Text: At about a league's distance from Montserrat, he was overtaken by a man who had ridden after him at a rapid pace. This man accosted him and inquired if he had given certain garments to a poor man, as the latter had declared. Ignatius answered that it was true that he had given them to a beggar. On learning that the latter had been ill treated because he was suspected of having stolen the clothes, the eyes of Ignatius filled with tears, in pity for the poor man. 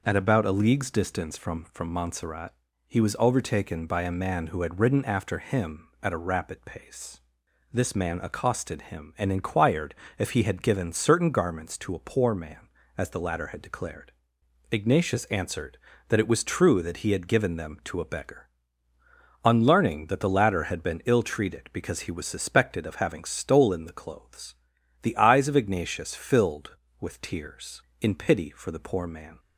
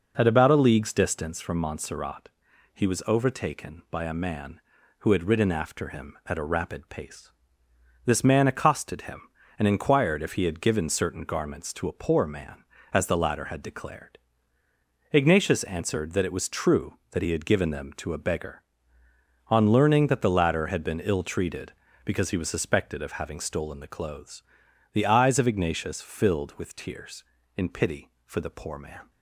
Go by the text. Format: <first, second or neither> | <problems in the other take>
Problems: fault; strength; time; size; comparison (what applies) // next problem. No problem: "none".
second | says "from" twice; at 1.7 s // pauses between "inquired" and "if"; slight; at 9.9 s; 0.22 s long